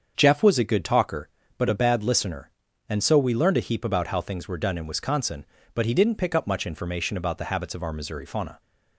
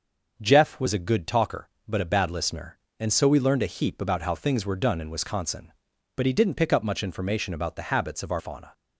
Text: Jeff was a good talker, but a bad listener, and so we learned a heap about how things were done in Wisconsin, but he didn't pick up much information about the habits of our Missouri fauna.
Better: first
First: starts louder than the rest; until 1.1 s; 7 dB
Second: starts louder than the rest; until 1.3 s; 6.5 dB // skips "Missouri"; at 8.3 s

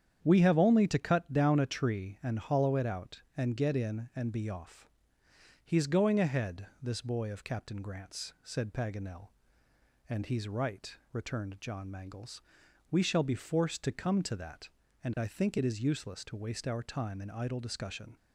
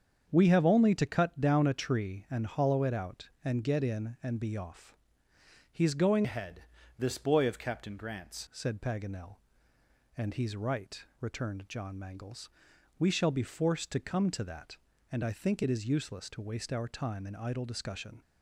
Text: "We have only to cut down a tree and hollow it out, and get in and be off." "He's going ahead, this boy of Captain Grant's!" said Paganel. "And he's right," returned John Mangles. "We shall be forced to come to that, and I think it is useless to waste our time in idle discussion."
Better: first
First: starts louder than the rest; strong; until 1.2 s; 8.5 dB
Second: starts louder than the rest; strong; until 1.3 s; 7 dB // changes voice from "ahead" to "Grant's"; from 6.2 to 8.4 s; 2.2 s long

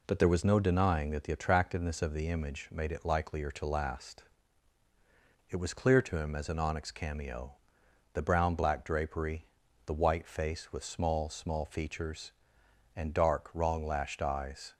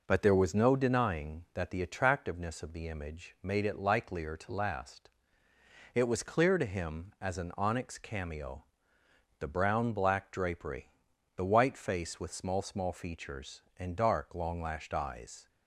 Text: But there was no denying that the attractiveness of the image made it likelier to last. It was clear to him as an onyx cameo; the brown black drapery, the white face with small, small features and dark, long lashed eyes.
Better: second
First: says "wrong" for "long"; at 13.5 s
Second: none

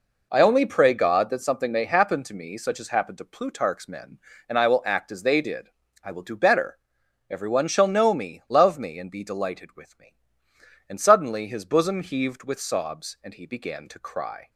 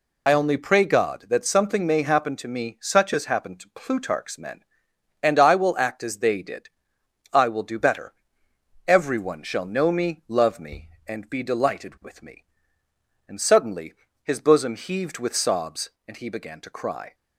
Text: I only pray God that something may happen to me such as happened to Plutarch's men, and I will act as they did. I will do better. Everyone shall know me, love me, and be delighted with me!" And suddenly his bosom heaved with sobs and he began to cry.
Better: first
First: none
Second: loses the start of "I"; at 0.2 s; 55 ms // pauses between "suddenly" and "his"; slight; at 13.9 s; 0.28 s long

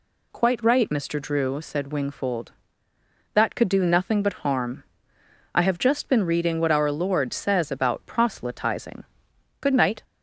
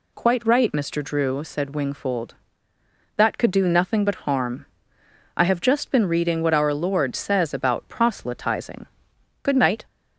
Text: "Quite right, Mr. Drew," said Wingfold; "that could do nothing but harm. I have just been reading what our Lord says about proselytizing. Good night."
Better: neither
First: none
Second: none

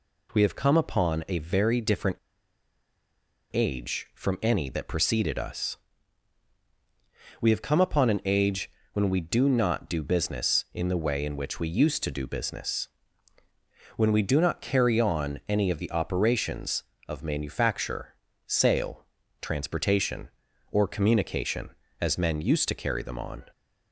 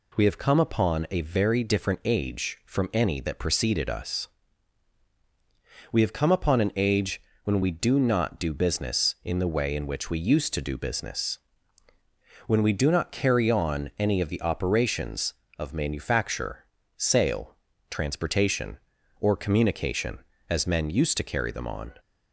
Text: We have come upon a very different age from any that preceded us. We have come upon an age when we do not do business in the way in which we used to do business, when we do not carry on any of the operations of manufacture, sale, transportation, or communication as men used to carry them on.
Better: second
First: pauses between "different" and "age"; strong; at 2.1 s; 1.3 s long // pauses between "age" and "when"; slight; at 8.6 s; 0.24 s long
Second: pauses between "age" and "when"; slight; at 7.2 s; 0.24 s long

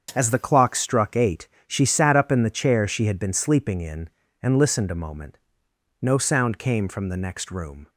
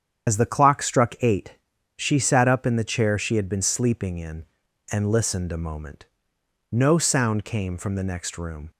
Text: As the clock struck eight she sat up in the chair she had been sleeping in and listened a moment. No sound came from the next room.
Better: first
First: starts louder than the rest; until 1.1 s; 7 dB // pauses between "eight" and "she"; slight; at 1.4 s; 0.20 s long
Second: loses the start of "As"; at 0.2 s; 70 ms // starts louder than the rest; strong; until 1.3 s; 8.5 dB // pauses between "eight" and "she"; at 1.5 s; 0.40 s long

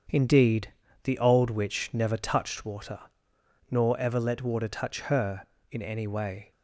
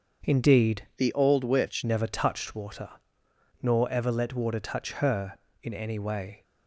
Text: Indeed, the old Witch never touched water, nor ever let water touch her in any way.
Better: first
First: starts louder than the rest; strong; until 1.4 s; 7.5 dB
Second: starts louder than the rest; until 1.3 s; 6.5 dB // changes voice from "the" to "Witch"; from 0.9 to 1.8 s; 0.9 s long

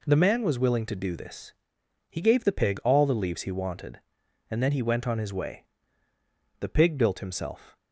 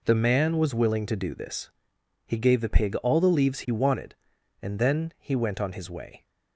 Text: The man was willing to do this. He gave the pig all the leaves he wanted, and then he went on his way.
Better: second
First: goes on to say "The pig built himself"; noticeable; from 6.5 s on; 1.2 s long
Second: none

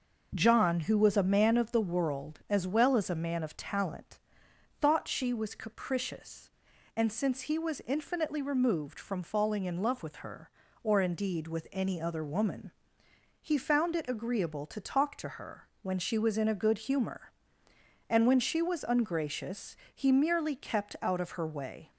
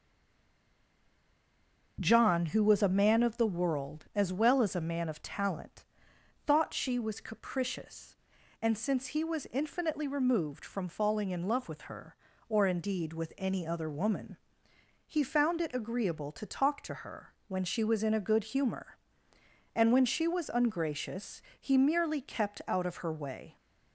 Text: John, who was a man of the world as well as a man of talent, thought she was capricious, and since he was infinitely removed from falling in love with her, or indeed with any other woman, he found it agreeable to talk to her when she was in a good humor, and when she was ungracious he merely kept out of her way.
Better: first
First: pauses between "her" and "when"; slight; at 15.6 s; 0.16 s long // pauses between "ungracious" and "he"; slight; at 19.7 s; 0.18 s long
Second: stays silent before the first word; noticeable; until 1.9 s; 1.9 s long // pauses between "her" and "when"; slight; at 17.3 s; 0.16 s long // pauses between "ungracious" and "he"; slight; at 21.4 s; 0.18 s long

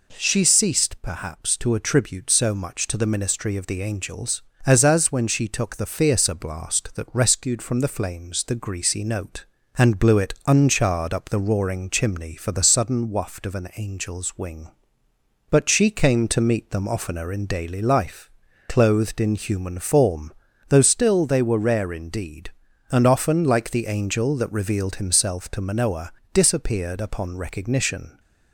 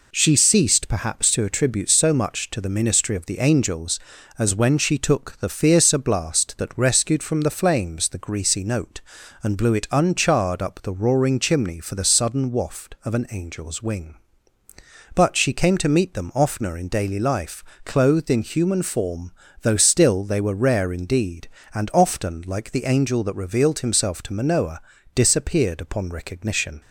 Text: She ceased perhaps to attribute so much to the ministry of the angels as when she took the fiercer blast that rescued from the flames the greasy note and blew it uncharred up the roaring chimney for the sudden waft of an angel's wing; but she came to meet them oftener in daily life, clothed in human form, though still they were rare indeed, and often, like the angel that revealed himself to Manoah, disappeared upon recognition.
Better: second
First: says "as" twice; at 4.8 s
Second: none

